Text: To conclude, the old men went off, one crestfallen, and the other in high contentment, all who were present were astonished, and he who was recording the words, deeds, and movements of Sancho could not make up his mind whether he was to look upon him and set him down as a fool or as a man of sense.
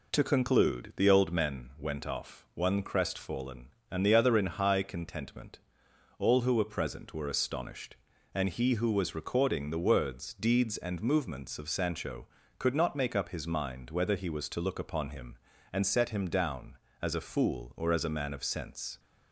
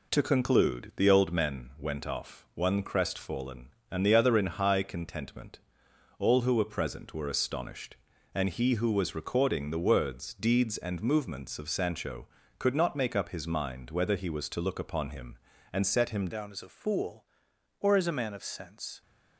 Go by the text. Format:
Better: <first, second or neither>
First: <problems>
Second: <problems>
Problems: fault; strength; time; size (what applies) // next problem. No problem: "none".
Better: first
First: none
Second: changes voice at "down"; from 16.3 s on; 2.7 s long